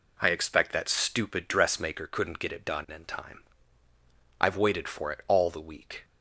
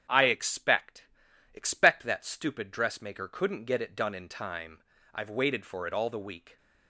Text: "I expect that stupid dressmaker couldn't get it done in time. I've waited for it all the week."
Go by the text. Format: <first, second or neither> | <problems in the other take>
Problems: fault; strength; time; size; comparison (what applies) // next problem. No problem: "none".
first | starts louder than the rest; strong; until 1.5 s; 8.5 dB // says "expect" twice; at 1.5 s